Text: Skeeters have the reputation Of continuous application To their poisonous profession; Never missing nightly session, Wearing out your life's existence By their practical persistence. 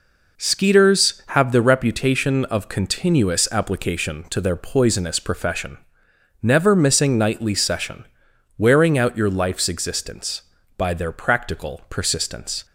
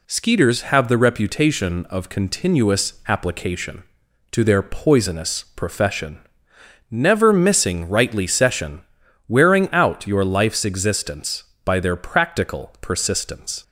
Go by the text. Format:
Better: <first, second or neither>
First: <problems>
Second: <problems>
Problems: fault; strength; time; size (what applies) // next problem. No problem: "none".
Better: first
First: none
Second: says "rightly" for "nightly"; at 7.8 s